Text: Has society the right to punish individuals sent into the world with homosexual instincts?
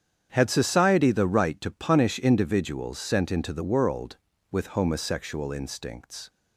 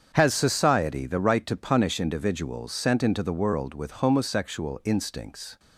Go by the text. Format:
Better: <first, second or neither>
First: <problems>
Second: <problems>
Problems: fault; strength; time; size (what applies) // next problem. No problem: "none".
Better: second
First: starts louder than the rest; strong; until 1.3 s; 8.5 dB // says "Had" for "Has"; at 0.3 s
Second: starts louder than the rest; strong; until 1.1 s; 7.5 dB